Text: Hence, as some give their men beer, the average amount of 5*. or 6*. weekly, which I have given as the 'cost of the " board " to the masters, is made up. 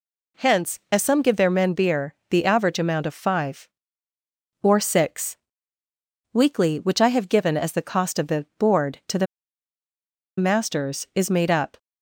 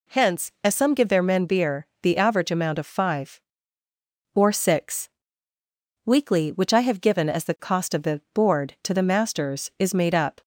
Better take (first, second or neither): second